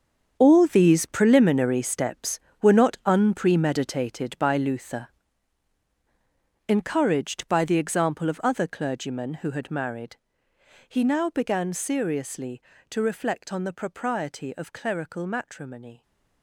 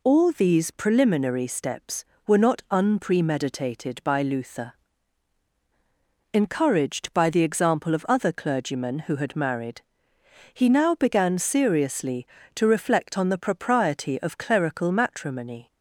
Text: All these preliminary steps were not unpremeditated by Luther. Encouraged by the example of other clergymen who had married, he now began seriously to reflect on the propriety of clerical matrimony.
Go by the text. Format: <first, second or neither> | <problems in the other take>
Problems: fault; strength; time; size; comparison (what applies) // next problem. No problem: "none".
second | gets quieter; strong; throughout; 12.5 dB